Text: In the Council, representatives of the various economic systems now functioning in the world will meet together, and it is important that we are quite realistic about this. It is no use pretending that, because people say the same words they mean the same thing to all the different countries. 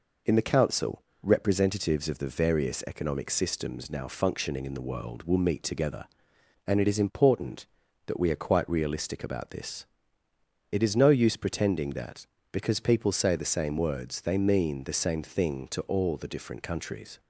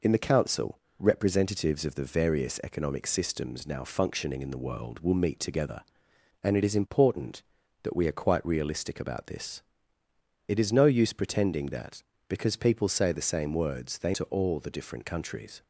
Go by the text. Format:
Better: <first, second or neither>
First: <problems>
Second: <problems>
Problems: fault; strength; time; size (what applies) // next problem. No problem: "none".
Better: first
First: none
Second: skips "mean the same thing"; at 14.1 s